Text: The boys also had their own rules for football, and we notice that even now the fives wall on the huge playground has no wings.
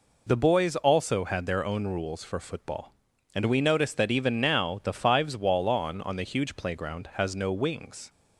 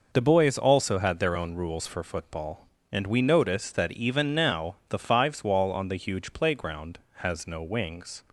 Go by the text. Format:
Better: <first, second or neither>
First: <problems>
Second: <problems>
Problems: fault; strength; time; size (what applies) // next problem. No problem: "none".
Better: second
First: says "on" twice; at 6.0 s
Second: none